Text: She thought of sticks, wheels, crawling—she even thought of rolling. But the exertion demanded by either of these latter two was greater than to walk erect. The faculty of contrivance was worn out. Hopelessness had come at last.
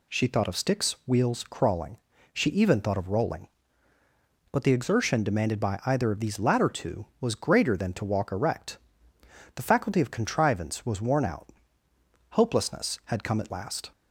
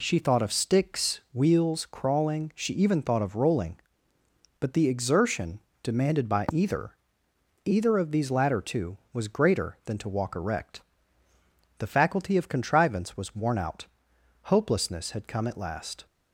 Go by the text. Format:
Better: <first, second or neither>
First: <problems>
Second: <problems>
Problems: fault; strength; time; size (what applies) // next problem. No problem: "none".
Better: first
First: none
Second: pauses between "exertion" and "demanded"; slight; at 5.5 s; 0.24 s long // says "either" twice; at 7.6 s